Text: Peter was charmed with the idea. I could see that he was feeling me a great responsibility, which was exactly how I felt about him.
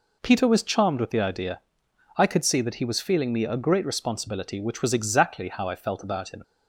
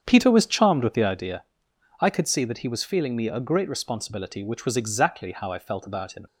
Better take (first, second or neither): first